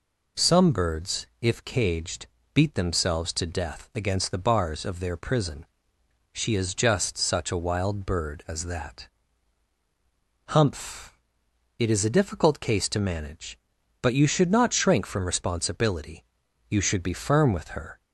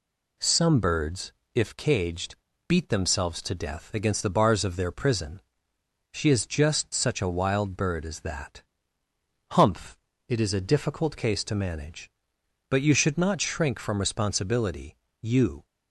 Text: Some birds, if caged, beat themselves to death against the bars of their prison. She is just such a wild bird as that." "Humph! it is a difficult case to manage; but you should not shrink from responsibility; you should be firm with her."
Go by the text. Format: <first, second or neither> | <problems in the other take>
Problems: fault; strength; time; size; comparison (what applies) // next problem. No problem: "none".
first | stops before "should be firm with her"; at 15.6 s